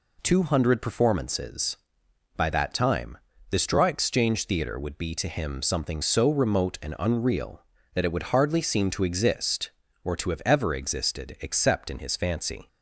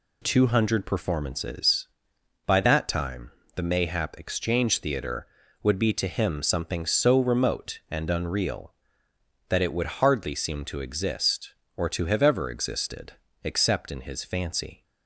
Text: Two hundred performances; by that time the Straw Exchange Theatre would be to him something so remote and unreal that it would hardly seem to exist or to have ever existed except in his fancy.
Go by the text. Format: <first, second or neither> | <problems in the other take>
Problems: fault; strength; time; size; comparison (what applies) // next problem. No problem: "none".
first | pauses between "time" and "the"; slight; at 3.3 s; 0.24 s long; slight in the first // says "Mayhap" for "Straw"; at 3.6 s // pauses between "existed" and "except"; slight; at 13.1 s; 0.30 s long